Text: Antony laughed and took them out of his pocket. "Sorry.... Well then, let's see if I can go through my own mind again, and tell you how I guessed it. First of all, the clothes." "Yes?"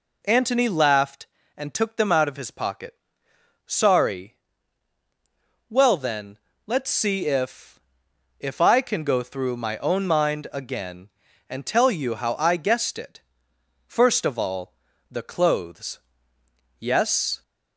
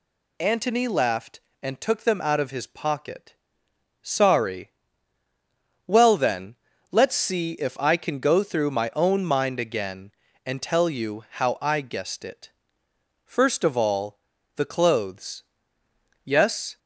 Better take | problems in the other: second | says "if" twice; at 8.3 s

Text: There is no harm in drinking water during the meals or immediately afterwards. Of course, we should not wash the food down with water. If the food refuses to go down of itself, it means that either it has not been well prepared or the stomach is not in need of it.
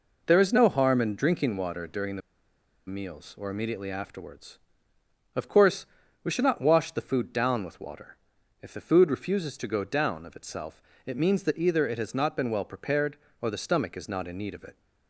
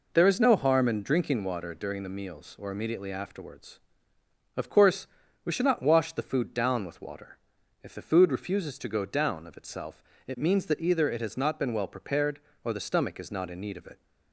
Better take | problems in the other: second | pauses between "the" and "meals"; noticeable; at 2.2 s; 0.67 s long

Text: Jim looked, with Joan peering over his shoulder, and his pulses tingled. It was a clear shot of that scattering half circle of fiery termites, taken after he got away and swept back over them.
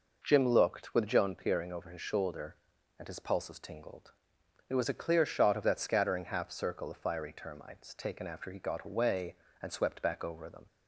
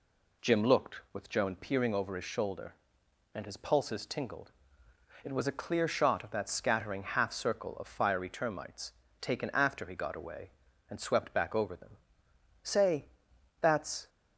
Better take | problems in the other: first | goes on to say "Say that's"; from 12.6 s on; 1.4 s long

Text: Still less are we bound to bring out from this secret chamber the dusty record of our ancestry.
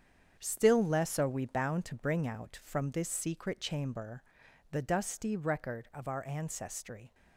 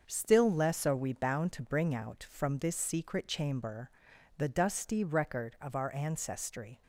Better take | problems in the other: second | gets quieter; strong; throughout; 9.5 dB // starts louder than the rest; strong; until 1.4 s; 8 dB; also in the second // pauses between "chamber" and "the"; noticeable; at 4.2 s; 0.48 s long; noticeable in the second

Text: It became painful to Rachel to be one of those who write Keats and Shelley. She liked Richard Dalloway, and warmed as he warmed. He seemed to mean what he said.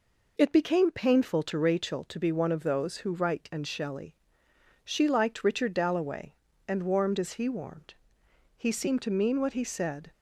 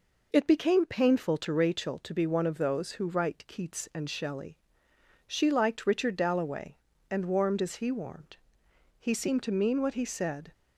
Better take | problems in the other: second | skips "Keats"; at 3.5 s

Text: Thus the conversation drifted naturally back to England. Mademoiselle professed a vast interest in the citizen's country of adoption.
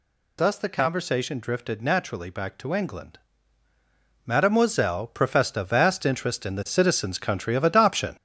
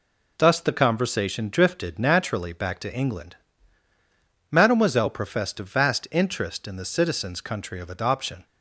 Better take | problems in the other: second | gets louder; noticeable; throughout; 6 dB

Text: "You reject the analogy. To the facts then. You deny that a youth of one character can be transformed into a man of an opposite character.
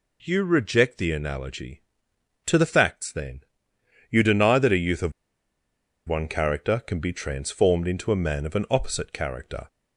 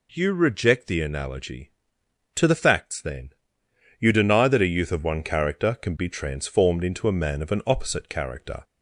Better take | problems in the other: second | pauses between "of" and "one"; noticeable; at 5.1 s; 0.97 s long

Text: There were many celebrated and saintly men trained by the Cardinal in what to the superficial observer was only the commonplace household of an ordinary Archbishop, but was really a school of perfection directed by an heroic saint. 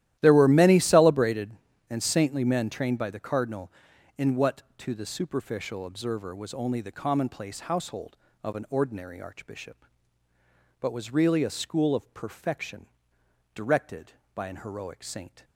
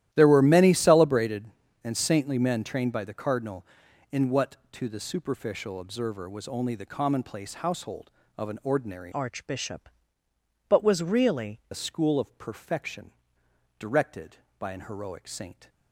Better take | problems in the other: first | starts louder than the rest; strong; until 1.1 s; 13 dB; strong in the first // changes voice from "Archbishop" to "really"; from 9.1 to 11.6 s; 2.5 s long // pauses between "perfection" and "directed"; noticeable; at 13.1 s; 0.68 s long; noticeable in the first

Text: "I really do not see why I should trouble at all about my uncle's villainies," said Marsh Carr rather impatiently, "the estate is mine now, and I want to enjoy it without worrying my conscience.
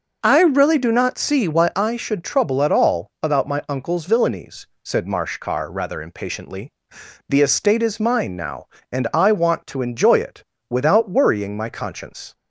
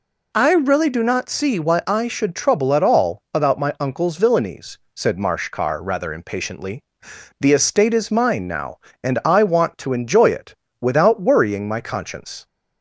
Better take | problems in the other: second | starts louder than the rest; noticeable; until 2.0 s; 5.5 dB // pauses between "it" and "without"; slight; at 10.4 s; 0.28 s long; slight in the second

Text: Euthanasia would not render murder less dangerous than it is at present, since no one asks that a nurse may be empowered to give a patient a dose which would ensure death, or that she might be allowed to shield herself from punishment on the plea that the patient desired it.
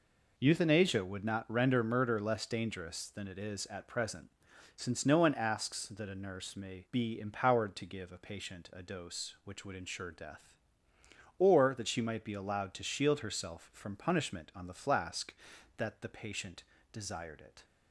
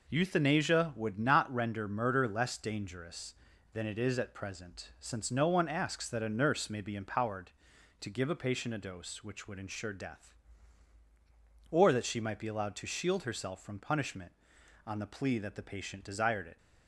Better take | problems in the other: second | says "flask" for "plea"; at 14.7 s // pauses between "patient" and "desired"; slight; at 16.6 s; 0.28 s long

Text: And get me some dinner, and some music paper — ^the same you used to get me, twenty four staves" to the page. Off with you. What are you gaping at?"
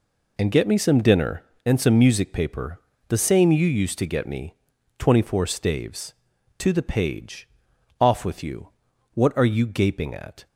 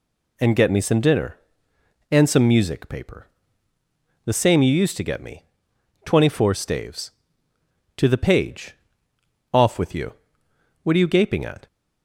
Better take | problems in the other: neither | none

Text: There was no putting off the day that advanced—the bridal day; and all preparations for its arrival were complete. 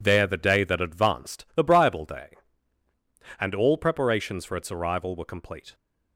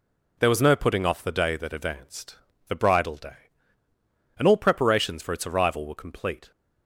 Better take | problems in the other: second | skips "was no putting off"; at 0.2 s

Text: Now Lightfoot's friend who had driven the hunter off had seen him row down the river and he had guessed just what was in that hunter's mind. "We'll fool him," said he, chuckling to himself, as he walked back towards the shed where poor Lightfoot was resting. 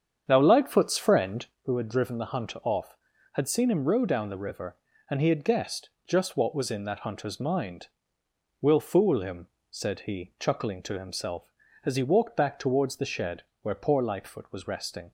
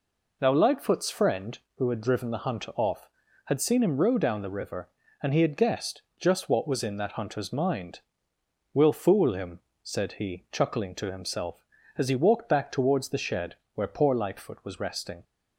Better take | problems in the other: second | starts louder than the rest; strong; until 1.7 s; 8 dB // pauses between "guessed" and "just"; slight; at 5.8 s; 0.18 s long; slight in the second // pauses between "shed" and "where"; slight; at 13.4 s; 0.20 s long; slight in the second

